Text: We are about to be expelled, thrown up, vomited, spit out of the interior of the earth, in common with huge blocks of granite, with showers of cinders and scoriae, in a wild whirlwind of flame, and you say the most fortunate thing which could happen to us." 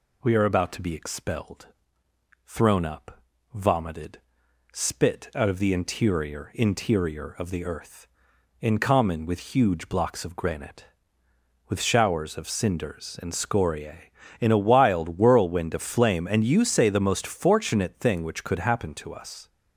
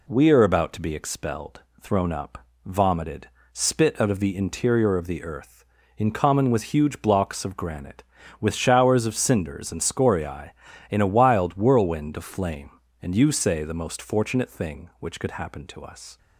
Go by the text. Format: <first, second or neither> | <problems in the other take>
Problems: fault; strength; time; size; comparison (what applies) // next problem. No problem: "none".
second | says "interior" twice; at 6.5 s